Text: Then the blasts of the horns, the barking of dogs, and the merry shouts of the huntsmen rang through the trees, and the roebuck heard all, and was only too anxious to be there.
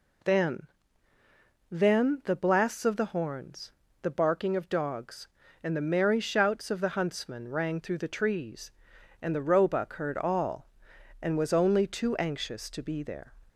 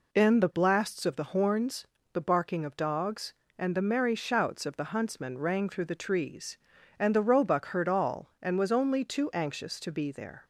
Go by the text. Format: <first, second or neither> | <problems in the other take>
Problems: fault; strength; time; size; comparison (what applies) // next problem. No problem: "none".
second | says "Then" twice; at 1.6 s